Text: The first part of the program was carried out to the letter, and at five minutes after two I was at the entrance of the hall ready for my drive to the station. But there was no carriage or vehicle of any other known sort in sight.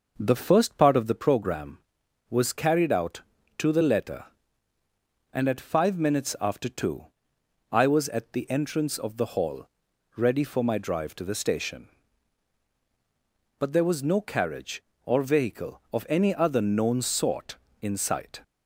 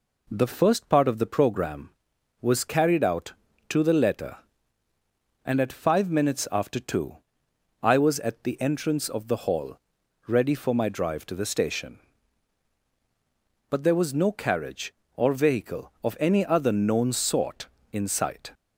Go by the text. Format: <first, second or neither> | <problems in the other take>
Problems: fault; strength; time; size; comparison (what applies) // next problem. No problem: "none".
second | starts louder than the rest; noticeable; until 1.1 s; 6 dB // pauses between "two" and "I"; noticeable; at 7.0 s; 0.62 s long; noticeable in the second // pauses between "hall" and "ready"; noticeable; at 9.6 s; 0.48 s long; noticeable in the second